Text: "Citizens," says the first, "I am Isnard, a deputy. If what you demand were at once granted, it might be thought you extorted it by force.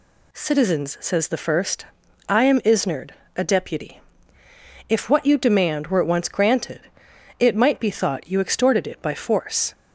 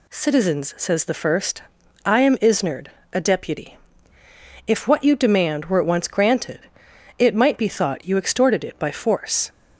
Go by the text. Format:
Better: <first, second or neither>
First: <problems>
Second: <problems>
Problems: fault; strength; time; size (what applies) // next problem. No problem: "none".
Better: neither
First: none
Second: none